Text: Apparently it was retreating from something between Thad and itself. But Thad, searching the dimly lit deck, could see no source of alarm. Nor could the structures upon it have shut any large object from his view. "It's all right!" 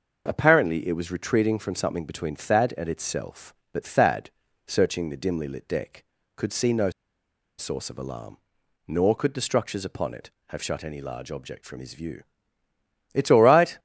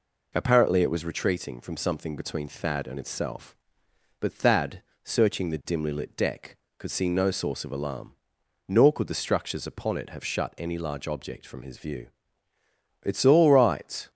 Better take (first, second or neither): second